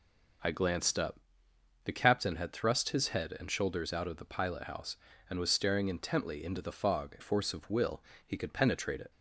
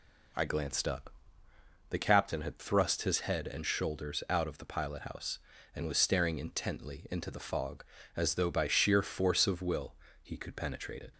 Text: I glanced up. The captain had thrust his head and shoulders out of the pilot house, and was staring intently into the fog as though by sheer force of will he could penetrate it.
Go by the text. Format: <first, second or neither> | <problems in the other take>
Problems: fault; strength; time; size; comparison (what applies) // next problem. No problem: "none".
second | skips "as though by sheer"; at 7.1 s // pauses between "will" and "he"; slight; at 8.0 s; 0.24 s long; slight in the second